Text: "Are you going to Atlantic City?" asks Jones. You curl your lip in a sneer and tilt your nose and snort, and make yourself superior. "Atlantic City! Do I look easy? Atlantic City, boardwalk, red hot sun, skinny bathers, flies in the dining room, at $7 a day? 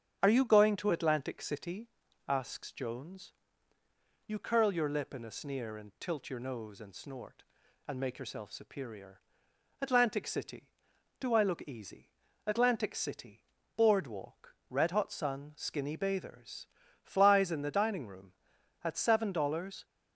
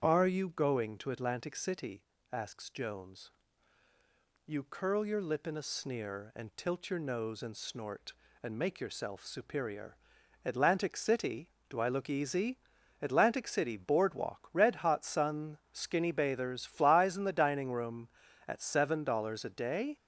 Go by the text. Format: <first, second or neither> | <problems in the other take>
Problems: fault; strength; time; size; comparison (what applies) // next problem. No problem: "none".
second | starts louder than the rest; strong; until 1.2 s; 8.5 dB; strong in the second // stops before "a day"; at 19.8 s